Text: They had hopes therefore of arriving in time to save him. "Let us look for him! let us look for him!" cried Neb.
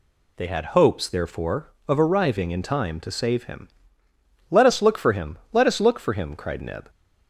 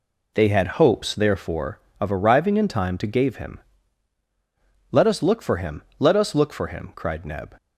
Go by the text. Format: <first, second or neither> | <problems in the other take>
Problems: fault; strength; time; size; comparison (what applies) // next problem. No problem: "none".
first | says "gave" for "save"; at 3.0 s